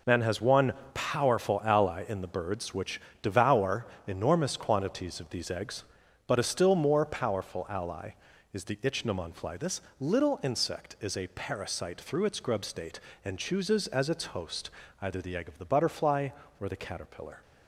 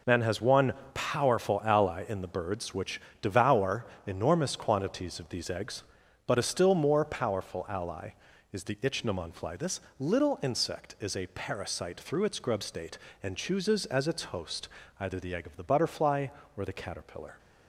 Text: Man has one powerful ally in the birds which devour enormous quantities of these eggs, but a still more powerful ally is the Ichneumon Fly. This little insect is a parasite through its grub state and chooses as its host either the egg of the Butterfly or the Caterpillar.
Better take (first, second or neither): neither